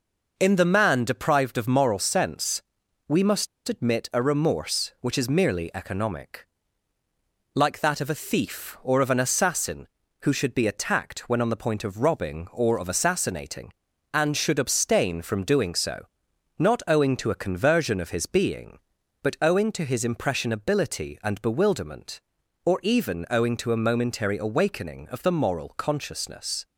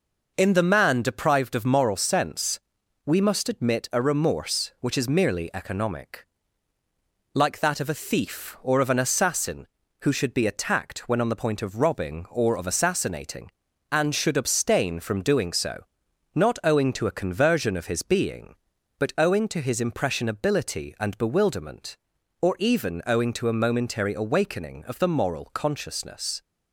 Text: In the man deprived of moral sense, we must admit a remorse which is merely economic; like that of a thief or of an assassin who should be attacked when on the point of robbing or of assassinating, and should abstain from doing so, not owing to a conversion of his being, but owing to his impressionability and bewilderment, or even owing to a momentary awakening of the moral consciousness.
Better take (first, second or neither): second